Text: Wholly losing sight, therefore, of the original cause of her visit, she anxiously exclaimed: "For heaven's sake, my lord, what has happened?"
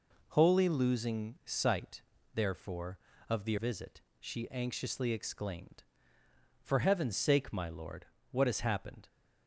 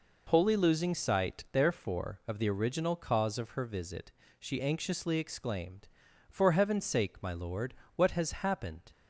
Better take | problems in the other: second | skips "original cause of her"; at 3.5 s

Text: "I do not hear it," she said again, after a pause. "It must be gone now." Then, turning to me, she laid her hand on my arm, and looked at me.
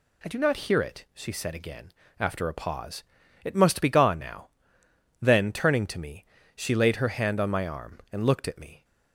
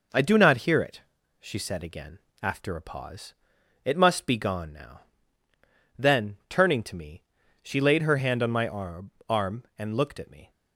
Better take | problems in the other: first | says "arm" twice; at 9.2 s

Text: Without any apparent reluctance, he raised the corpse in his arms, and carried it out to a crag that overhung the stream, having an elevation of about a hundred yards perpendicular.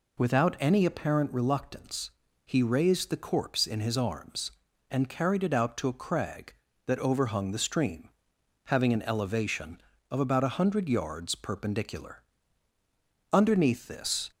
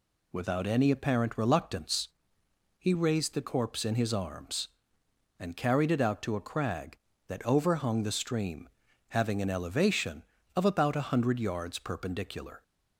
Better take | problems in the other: second | goes on to say "Underneath this"; noticeable; from 13.3 s on; 1.0 s long

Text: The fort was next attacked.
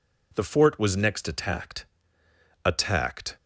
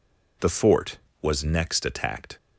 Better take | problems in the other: second | says "attacked" twice; at 2.6 s

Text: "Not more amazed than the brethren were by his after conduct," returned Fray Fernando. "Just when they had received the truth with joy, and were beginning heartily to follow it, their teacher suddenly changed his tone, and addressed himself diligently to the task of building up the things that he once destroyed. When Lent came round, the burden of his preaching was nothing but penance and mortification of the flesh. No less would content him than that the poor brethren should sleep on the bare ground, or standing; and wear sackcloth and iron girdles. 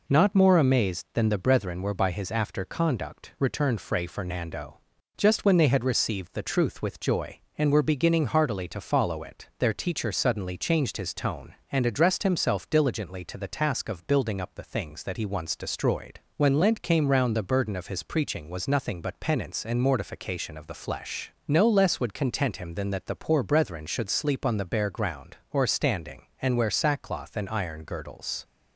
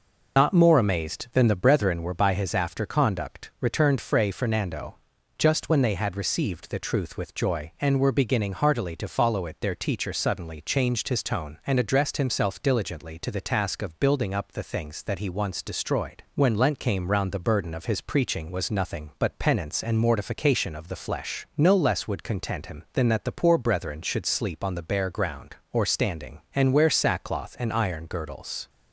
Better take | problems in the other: first | loses the start of "Not"; at 0.3 s; 125 ms

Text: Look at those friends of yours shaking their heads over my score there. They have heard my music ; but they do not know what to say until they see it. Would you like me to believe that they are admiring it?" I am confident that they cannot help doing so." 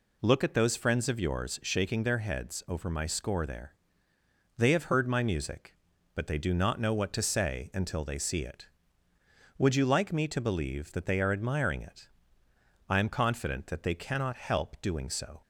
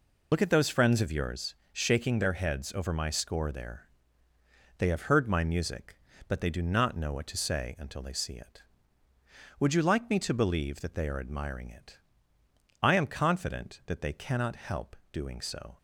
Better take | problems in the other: first | loses the start of "Look"; at 0.3 s; 55 ms // pauses between "yours" and "shaking"; slight; at 1.5 s; 0.18 s long // pauses between "help" and "doing"; slight; at 14.9 s; 0.16 s long

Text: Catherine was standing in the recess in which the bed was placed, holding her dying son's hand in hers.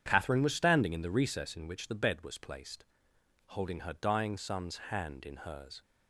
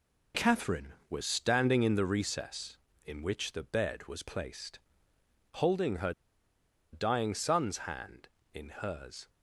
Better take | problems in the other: first | pauses between "her" and "dying"; noticeable; at 6.1 s; 0.80 s long

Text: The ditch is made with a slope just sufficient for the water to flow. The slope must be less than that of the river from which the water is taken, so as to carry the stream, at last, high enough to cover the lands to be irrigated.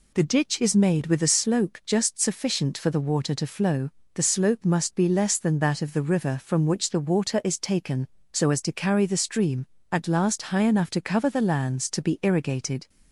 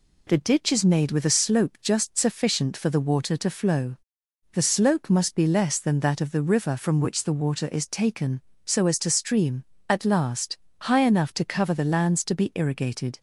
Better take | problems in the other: first | skips "carry the"; at 9.0 s

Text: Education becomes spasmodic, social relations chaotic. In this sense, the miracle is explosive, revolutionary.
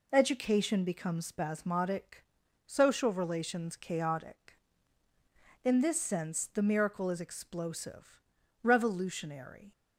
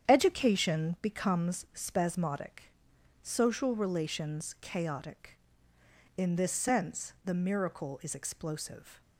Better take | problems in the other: first | starts louder than the rest; strong; until 1.1 s; 8.5 dB // stops before "revolutionary"; at 9.0 s

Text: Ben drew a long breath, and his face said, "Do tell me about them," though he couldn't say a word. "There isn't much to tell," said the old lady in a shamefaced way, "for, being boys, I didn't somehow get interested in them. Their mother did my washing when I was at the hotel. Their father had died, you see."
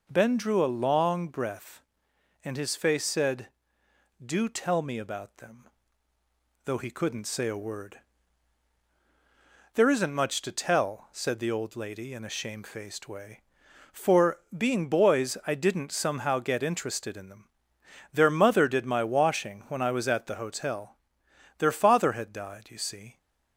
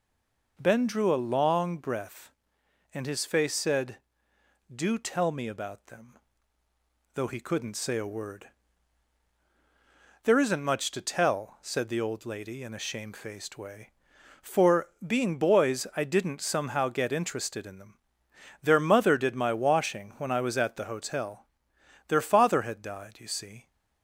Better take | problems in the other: first | stays silent before the first word; slight; until 0.5 s; 0.5 s long

